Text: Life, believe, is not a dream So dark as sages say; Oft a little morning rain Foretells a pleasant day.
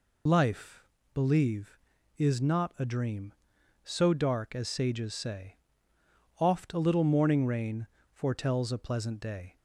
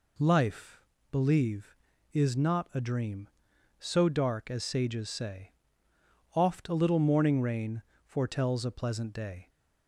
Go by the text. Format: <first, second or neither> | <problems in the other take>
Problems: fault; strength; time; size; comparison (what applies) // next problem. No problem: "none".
second | loses the start of "Life"; at 0.2 s; 55 ms // pauses between "rain" and "Foretells"; slight; at 7.8 s; 0.26 s long; slight in the second